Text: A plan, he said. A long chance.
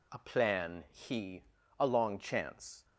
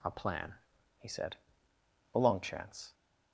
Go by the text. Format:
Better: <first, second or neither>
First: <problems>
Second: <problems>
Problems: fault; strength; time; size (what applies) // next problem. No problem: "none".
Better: second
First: skips "said"; at 1.6 s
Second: none